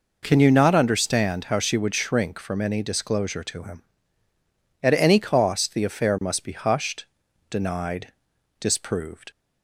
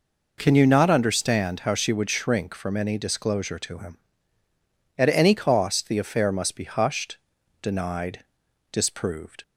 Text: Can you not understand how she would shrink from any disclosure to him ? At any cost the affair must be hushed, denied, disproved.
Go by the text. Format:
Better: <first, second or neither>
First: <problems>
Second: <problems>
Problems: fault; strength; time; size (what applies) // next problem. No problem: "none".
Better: neither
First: none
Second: none